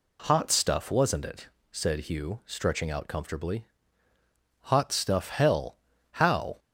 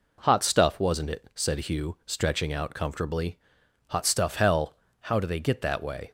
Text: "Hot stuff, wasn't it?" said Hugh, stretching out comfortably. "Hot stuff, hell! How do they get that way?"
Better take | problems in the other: second | stops before "do they get that way"; at 6.5 s

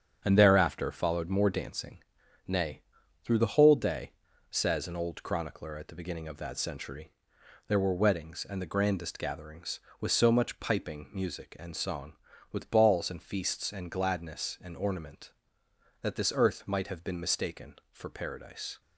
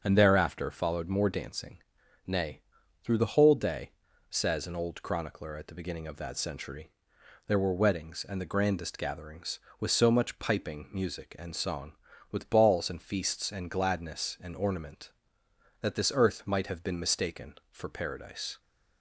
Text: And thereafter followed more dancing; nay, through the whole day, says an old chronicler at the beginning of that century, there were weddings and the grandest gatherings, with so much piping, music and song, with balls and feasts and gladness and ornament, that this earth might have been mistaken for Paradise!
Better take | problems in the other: second | gets quieter; throughout; 7 dB // starts louder than the rest; strong; until 1.2 s; 8 dB; also in the second

